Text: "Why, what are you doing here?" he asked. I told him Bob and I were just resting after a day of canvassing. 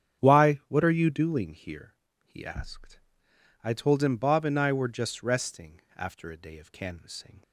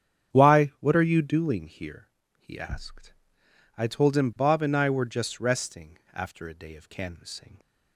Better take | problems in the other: neither | starts louder than the rest; strong; the same in both

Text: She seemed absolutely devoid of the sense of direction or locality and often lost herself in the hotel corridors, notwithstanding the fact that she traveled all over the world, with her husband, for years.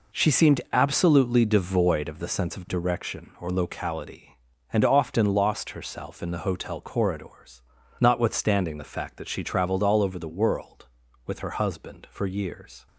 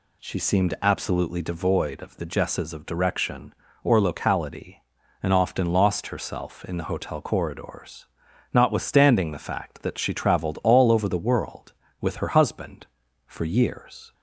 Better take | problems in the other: first | says "jesses" for "sense"; at 2.2 s

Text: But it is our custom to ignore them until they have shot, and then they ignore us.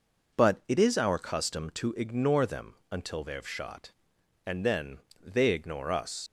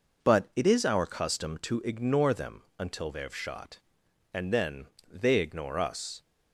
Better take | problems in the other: second | pauses between "them" and "until"; slight; at 2.7 s; 0.16 s long; slight in the second // pauses between "then" and "they"; slight; at 4.9 s; 0.22 s long; slight in the second // leaves "us" unfinished; at 6.2 s; 85 ms

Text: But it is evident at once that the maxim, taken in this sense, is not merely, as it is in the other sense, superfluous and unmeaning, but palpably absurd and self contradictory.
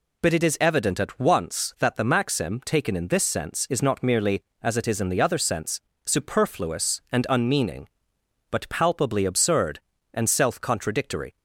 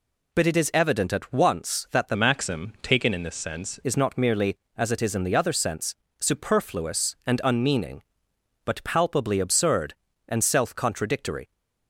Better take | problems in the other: first | changes voice from "maxim" to "sense"; from 2.1 to 3.7 s; 1.6 s long

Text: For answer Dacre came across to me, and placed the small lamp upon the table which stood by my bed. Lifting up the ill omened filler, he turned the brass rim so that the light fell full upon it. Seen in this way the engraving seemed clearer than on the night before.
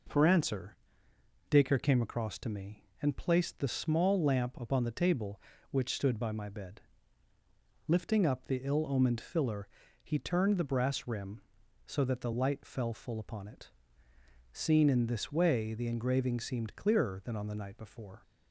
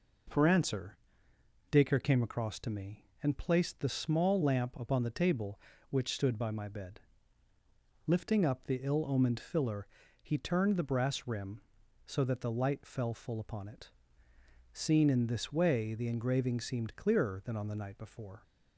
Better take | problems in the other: neither | pauses between "answer" and "Dacre"; noticeable; the same in both

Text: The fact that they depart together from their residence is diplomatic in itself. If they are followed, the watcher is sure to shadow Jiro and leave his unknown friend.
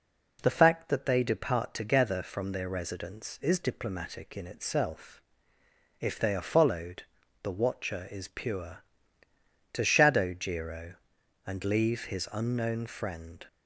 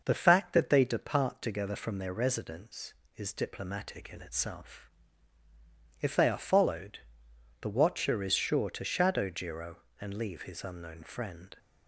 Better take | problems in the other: second | says "pure" for "sure"; at 8.2 s

